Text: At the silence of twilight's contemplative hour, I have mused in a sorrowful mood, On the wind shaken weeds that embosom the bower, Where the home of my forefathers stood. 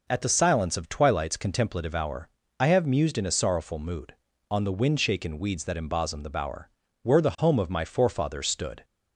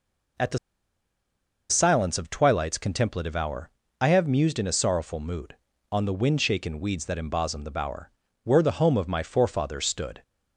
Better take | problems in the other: first | pauses between "the" and "silence"; at 0.5 s; 1.1 s long

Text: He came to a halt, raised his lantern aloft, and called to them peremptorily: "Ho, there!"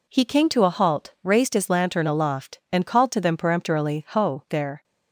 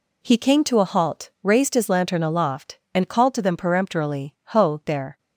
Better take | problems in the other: neither | none

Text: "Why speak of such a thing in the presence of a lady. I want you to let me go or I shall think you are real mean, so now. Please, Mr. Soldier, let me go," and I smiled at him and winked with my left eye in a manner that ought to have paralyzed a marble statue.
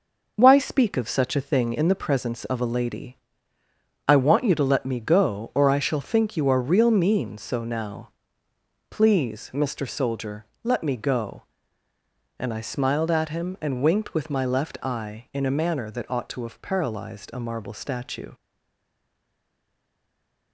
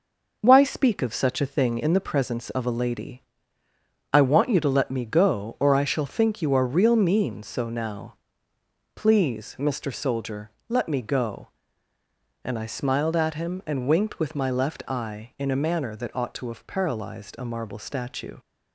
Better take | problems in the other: second | stays silent after the last word; from 18.3 s on; 2.2 s long

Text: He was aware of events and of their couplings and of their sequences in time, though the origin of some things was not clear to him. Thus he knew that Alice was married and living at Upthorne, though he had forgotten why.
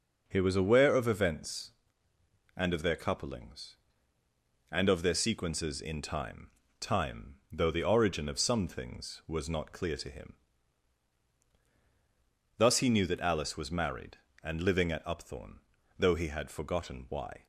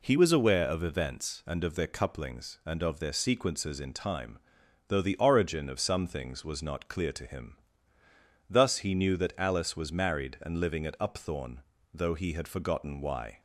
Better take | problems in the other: second | says "time" twice; at 6.8 s

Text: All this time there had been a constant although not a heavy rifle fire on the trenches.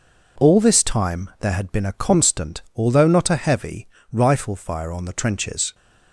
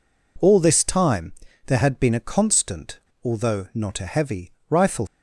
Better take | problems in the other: first | pauses between "time" and "there"; slight; at 1.3 s; 0.32 s long // pauses between "constant" and "although"; slight; at 2.9 s; 0.22 s long // pauses between "heavy" and "rifle"; slight; at 4.5 s; 0.18 s long; slight in the first // stops before "fire on the trenches"; at 5.0 s

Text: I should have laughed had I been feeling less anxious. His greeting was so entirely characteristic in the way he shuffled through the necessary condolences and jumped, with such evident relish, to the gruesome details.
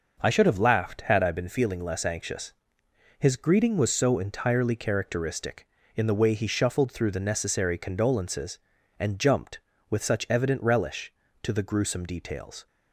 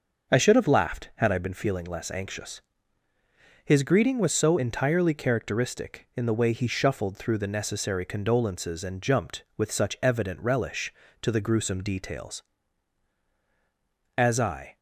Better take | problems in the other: first | starts louder than the rest; until 1.3 s; 6.5 dB // goes on to say "As I"; from 14.1 s on; 0.60 s long

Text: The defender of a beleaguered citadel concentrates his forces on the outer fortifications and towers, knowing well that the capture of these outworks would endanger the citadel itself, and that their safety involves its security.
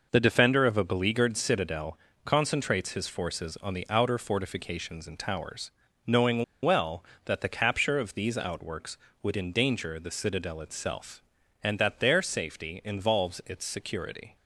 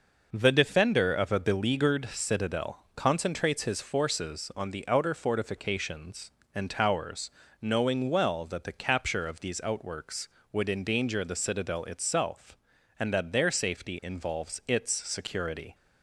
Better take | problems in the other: second | pauses between "citadel" and "concentrates"; slight; at 1.9 s; 0.26 s long // pauses between "knowing" and "well"; slight; at 6.4 s; 0.19 s long

